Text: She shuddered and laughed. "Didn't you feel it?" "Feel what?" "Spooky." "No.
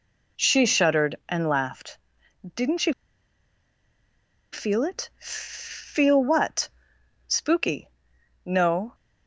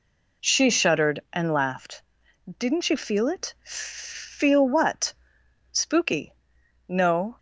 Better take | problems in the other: second | pauses between "you" and "feel"; strong; at 2.9 s; 1.6 s long

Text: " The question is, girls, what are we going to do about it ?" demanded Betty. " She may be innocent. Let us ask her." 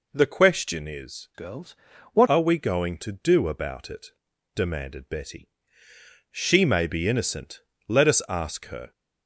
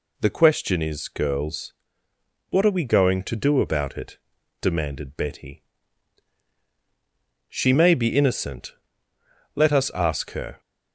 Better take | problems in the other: second | changes voice from "girls" to "what"; from 1.3 to 2.2 s; 0.9 s long

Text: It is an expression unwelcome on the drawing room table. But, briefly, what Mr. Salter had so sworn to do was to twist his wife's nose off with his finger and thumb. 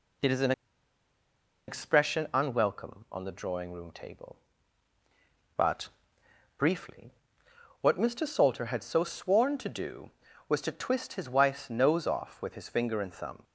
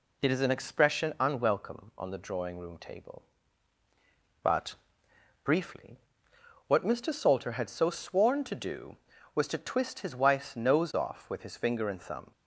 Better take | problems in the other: second | pauses between "an" and "expression"; at 0.5 s; 1.1 s long

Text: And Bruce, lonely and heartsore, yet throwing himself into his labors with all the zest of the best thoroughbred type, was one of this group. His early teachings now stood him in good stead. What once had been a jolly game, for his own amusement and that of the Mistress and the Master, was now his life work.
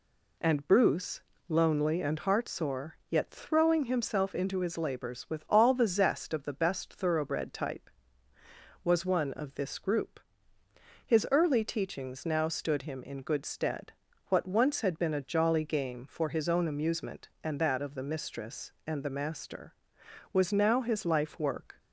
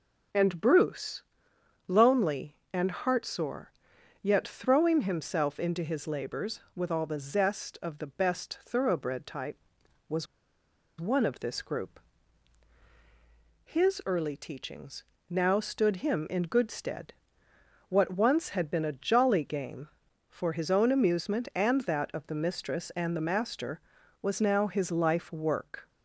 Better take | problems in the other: first | pauses between "was" and "one"; noticeable; at 10.2 s; 0.75 s long // pauses between "teachings" and "now"; slight; at 15.0 s; 0.26 s long

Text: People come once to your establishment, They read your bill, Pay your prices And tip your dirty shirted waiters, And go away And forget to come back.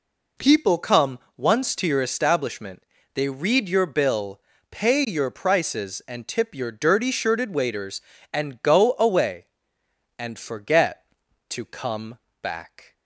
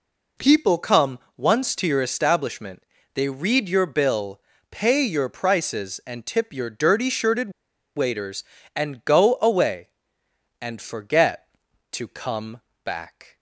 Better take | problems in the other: first | pauses between "come" and "once"; slight; at 1.1 s; 0.18 s long; slight in the first // pauses between "shirted" and "waiters"; at 7.5 s; 0.44 s long // pauses between "come" and "back"; slight; at 12.6 s; 0.24 s long; slight in the first

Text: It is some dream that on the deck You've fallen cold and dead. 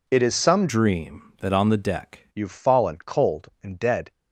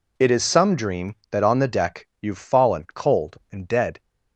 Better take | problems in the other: second | changes voice from "dream" to "deck"; from 0.6 to 2.2 s; 1.6 s long

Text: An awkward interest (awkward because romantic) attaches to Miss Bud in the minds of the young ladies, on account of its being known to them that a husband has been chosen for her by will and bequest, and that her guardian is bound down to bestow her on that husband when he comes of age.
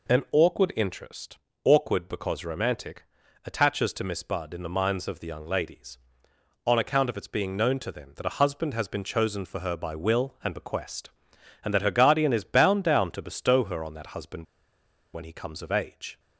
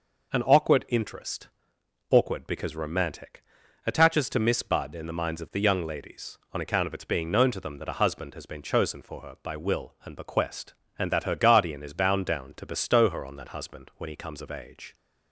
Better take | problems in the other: second | pauses between "husband" and "when"; noticeable; at 14.4 s; 0.68 s long

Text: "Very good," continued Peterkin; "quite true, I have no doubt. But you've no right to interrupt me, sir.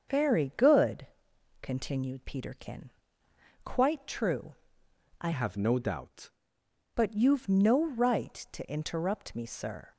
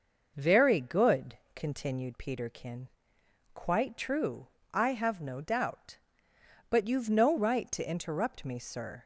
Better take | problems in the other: second | starts louder than the rest; until 1.6 s; 6.5 dB // changes voice from "have" to "doubt"; from 5.3 to 6.2 s; 0.9 s long

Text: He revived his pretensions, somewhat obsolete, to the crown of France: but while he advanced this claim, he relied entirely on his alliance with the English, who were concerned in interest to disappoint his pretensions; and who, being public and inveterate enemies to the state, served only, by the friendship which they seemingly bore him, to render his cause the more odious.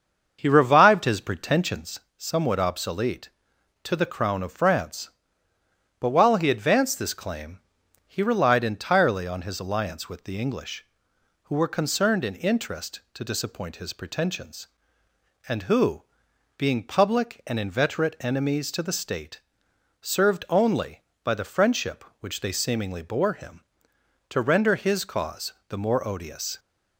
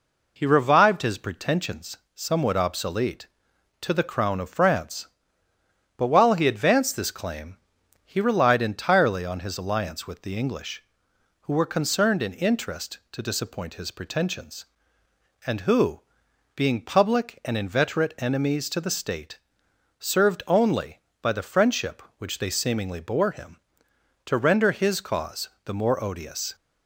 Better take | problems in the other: second | starts louder than the rest; until 2.1 s; 6.5 dB // pauses between "cause" and "the"; slight; at 25.5 s; 0.16 s long; slight in the second

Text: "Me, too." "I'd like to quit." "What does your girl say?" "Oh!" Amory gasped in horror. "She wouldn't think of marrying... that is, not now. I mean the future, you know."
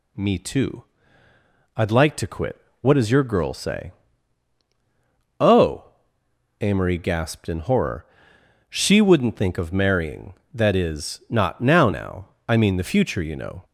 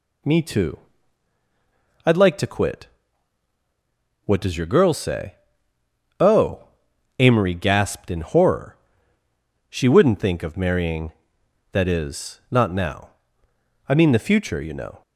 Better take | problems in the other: second | says "now" twice; at 11.9 s

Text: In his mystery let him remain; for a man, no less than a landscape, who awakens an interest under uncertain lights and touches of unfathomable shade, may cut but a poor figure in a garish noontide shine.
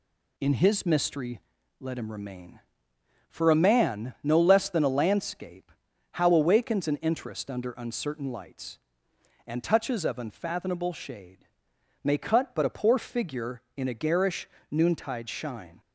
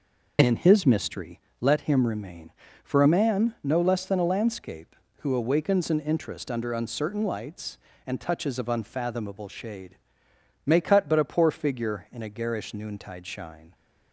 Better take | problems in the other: second | pauses between "mystery" and "let"; at 1.4 s; 0.40 s long; slight in the second // says "how" for "who"; at 6.1 s // pauses between "garish" and "noontide"; slight; at 14.4 s; 0.22 s long

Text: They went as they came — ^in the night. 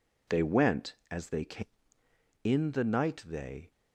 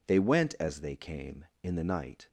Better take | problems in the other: second | goes on to say "They"; slight; from 3.2 s on; 0.44 s long

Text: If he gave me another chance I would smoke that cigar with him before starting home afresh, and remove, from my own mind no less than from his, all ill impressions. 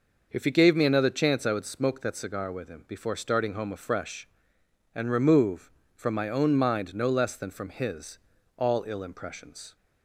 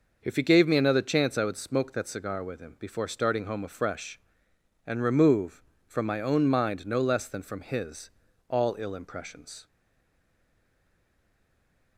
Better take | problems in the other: first | stays silent after the last word; from 9.6 s on; 2.3 s long

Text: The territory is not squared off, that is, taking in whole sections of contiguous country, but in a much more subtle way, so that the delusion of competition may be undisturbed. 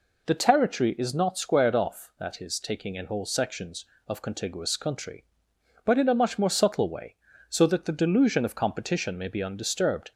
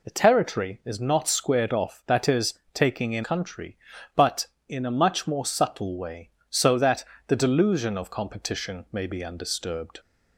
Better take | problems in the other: first | skips "whole sections of contiguous"; at 3.2 s // pauses between "that" and "the"; slight; at 7.0 s; 0.24 s long

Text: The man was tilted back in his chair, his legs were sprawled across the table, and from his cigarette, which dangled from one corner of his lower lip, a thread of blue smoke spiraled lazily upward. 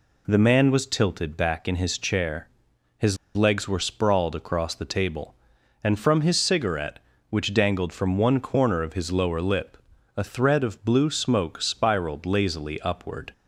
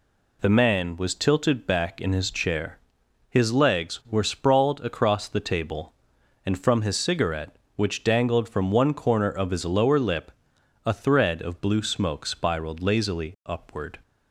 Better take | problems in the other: second | pauses between "his" and "legs"; slight; at 3.1 s; 0.20 s long

